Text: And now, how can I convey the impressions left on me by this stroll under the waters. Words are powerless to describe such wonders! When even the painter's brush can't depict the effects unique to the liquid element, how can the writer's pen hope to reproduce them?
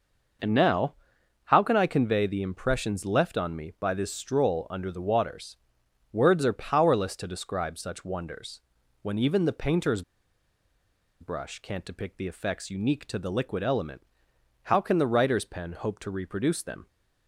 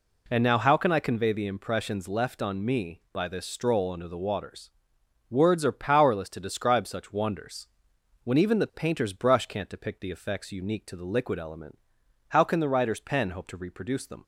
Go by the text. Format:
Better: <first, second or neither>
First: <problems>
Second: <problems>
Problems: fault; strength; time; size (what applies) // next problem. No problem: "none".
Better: second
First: pauses between "painter's" and "brush"; at 10.0 s; 1.1 s long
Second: none